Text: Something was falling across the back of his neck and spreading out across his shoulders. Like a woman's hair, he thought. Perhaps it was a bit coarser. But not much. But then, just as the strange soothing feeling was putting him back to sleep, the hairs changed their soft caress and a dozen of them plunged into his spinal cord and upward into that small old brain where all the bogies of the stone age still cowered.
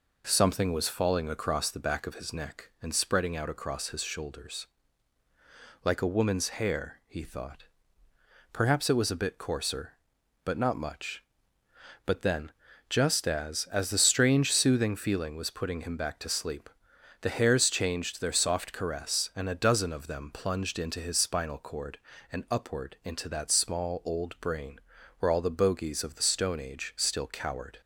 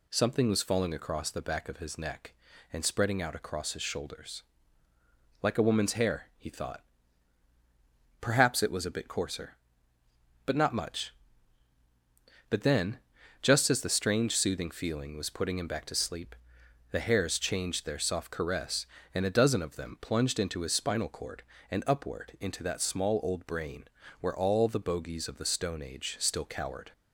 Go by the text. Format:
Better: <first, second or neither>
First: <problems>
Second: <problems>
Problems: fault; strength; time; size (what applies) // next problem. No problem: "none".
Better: second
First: says "as" twice; at 13.7 s // pauses between "brain" and "where"; at 24.7 s; 0.40 s long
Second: pauses between "brain" and "where"; slight; at 23.8 s; 0.36 s long